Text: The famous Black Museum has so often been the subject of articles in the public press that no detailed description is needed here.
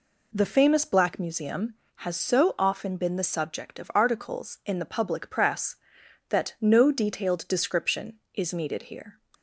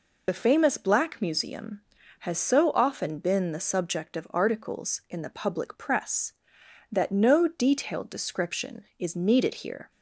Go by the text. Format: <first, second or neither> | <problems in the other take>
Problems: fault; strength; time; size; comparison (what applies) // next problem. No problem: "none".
first | loses the start of "The"; at 0.2 s; 35 ms